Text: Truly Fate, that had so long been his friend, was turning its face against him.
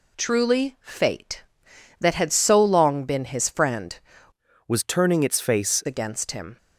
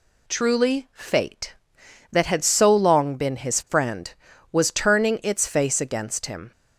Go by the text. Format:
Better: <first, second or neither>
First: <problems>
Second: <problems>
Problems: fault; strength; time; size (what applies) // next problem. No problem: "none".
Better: second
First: changes voice from "was" to "face"; from 4.6 to 5.8 s; 1.2 s long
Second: none